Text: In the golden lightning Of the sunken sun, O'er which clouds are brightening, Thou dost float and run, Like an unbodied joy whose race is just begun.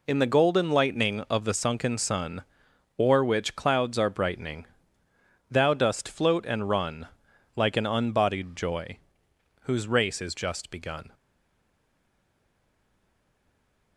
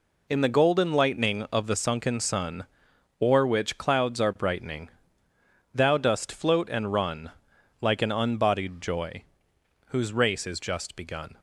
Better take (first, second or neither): second